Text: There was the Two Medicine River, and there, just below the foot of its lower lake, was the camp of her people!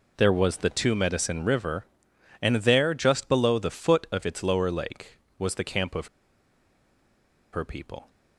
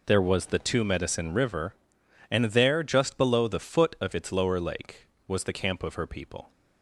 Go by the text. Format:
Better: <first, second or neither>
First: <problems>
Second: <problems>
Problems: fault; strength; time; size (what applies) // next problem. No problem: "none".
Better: second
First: pauses between "of" and "her"; strong; at 6.0 s; 1.4 s long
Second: none